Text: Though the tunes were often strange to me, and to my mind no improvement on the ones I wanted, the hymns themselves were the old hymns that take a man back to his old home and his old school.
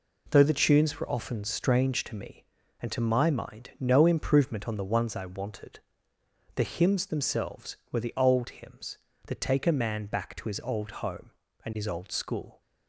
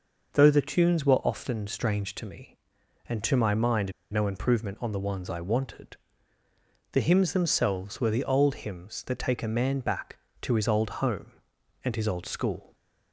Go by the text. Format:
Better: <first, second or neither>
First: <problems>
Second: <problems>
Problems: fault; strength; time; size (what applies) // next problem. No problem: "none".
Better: first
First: none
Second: pauses between "mind" and "no"; slight; at 3.9 s; 0.21 s long